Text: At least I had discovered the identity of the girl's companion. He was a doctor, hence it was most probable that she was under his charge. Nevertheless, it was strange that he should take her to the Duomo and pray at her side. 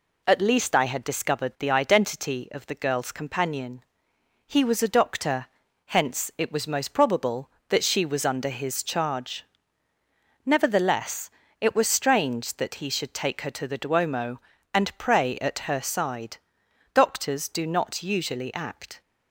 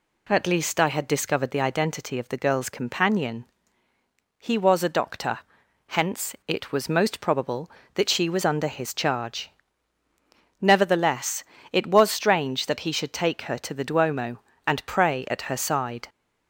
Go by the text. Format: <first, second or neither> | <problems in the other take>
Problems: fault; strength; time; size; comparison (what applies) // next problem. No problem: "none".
second | goes on to say "Doctors do not usually act"; strong; from 16.9 s on; 2.0 s long